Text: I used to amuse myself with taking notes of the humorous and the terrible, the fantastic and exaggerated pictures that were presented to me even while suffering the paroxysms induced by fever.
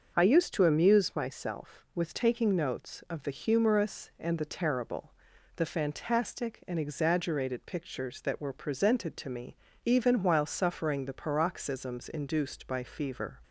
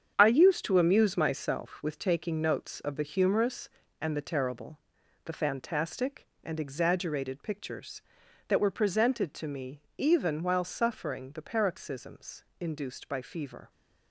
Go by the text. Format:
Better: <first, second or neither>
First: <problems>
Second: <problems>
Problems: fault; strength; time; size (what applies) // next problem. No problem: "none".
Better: first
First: starts louder than the rest; noticeable; until 1.1 s; 6 dB // pauses between "me" and "even"; slight; at 9.5 s; 0.28 s long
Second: gets quieter; strong; throughout; 9 dB // starts louder than the rest; strong; until 1.1 s; 8 dB // pauses between "me" and "even"; slight; at 9.7 s; 0.18 s long // pauses between "paroxysms" and "induced"; slight; at 12.4 s; 0.16 s long